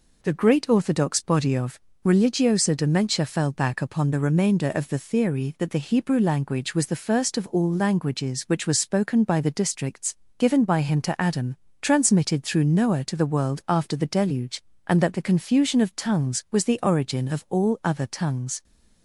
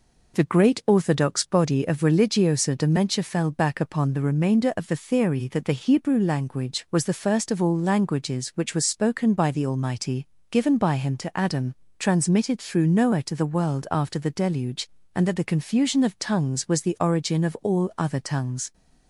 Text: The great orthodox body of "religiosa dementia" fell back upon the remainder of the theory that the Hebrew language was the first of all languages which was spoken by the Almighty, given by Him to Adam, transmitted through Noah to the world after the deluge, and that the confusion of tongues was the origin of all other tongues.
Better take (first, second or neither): second